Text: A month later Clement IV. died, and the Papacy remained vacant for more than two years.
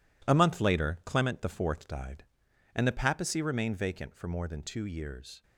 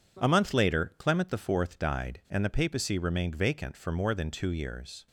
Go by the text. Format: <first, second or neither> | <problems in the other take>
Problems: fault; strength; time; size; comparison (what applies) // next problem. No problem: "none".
second | gets quieter; strong; throughout; 10.5 dB